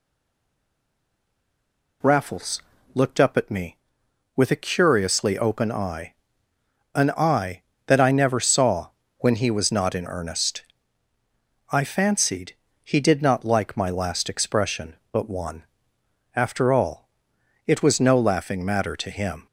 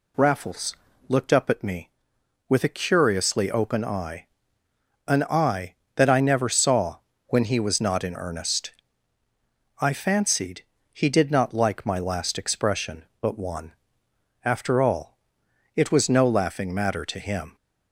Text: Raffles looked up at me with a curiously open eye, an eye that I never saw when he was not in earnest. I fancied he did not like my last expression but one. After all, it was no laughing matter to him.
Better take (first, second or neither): second